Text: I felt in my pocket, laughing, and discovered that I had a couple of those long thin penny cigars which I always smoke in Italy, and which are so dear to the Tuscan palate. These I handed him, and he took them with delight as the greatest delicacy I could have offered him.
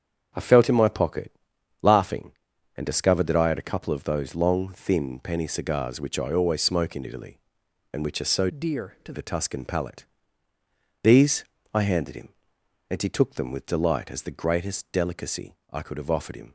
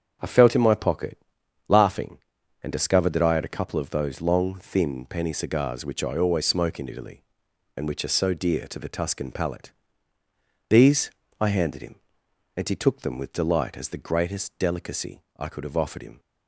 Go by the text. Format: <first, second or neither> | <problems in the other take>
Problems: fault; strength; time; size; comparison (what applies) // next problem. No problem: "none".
second | starts louder than the rest; strong; until 1.8 s; 7.5 dB; strong in the second // changes voice from "dear" to "to"; from 8.5 to 9.1 s; 0.6 s long // pauses between "These" and "I"; slight; at 11.4 s; 0.28 s long; slight in the second // pauses between "delicacy" and "I"; slight; at 15.5 s; 0.16 s long; slight in the second